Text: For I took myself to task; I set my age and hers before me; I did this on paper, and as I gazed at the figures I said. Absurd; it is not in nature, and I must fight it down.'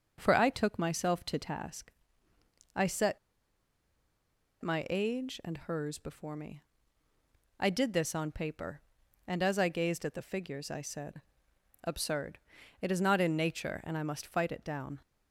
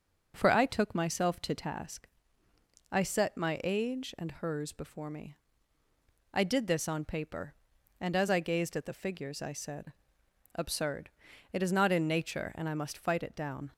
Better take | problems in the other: second | starts louder than the rest; until 1.1 s; 6.5 dB; also in the second // pauses between "set" and "my"; strong; at 3.1 s; 1.4 s long

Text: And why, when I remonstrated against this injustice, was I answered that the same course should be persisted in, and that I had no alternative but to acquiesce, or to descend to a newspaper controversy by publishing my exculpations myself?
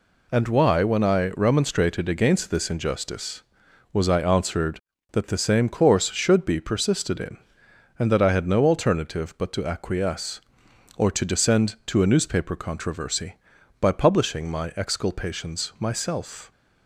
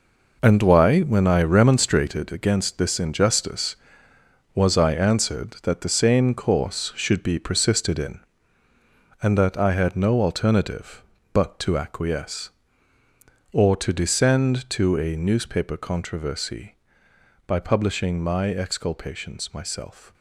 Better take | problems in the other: first | gets quieter; strong; throughout; 10.5 dB

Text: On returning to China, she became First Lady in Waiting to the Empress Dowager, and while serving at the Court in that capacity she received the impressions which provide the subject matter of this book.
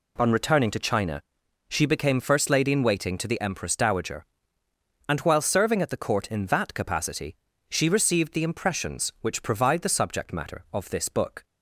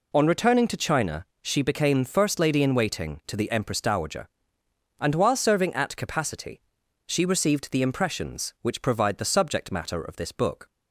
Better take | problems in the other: first | skips "the Court in that"; at 5.9 s // pauses between "capacity" and "she"; at 6.6 s; 0.44 s long; slight in the first

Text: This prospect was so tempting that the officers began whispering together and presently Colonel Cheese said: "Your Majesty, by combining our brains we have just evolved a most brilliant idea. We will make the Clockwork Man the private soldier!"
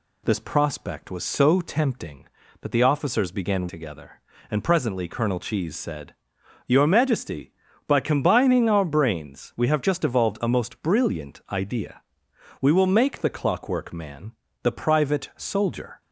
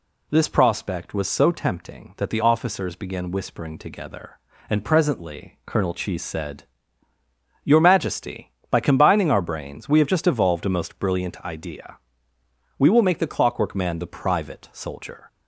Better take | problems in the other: second | skips "whispering"; at 3.6 s // pauses between "Man" and "the"; slight; at 14.3 s; 0.32 s long

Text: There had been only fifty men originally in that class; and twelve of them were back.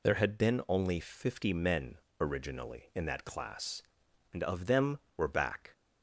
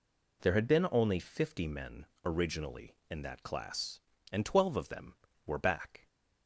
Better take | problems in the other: second | pauses between "men" and "originally"; slight; at 1.9 s; 0.22 s long; slight in the second // skips "twelve"; at 4.4 s

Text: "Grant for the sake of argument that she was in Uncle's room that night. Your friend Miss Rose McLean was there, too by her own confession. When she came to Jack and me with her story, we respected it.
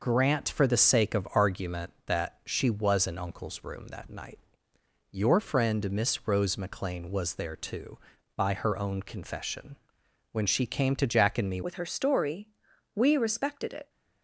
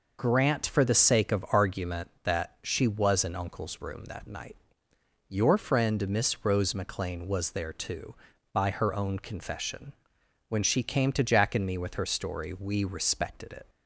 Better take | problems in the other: second | changes voice at "with"; from 11.6 s on; 2.2 s long

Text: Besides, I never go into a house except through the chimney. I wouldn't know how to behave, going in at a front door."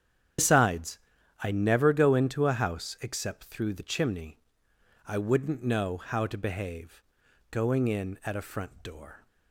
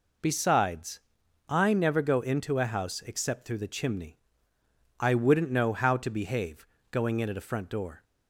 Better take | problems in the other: second | loses the start of "Besides"; at 0.3 s; 125 ms // starts louder than the rest; strong; until 1.8 s; 9 dB

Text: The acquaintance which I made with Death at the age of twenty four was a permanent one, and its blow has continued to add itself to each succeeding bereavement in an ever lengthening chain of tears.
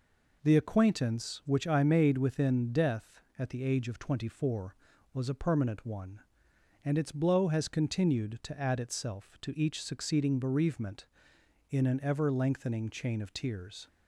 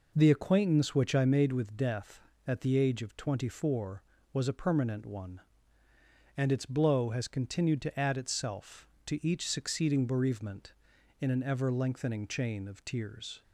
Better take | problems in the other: second | says "within" for "with"; at 2.1 s

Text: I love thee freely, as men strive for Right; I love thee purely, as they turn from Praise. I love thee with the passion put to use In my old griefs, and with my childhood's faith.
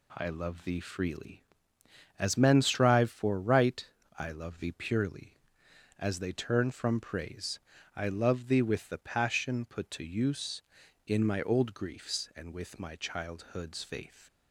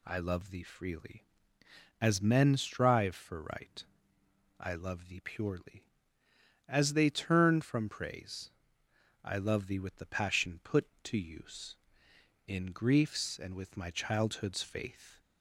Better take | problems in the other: first | skips "my old"; at 12.7 s

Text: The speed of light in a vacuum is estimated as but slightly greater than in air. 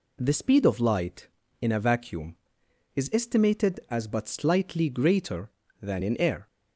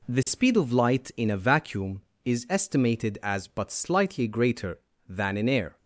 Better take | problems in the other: neither | none

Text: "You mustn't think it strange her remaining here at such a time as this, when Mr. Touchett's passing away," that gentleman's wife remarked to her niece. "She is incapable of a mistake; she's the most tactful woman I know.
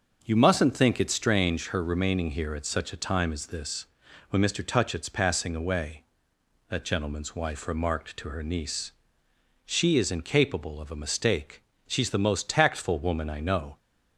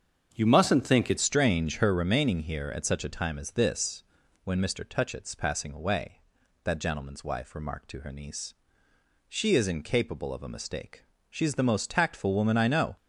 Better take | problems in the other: first | starts louder than the rest; strong; until 1.3 s; 7 dB; also in the first // changes voice at "strange"; from 1.1 s on; 11.8 s long

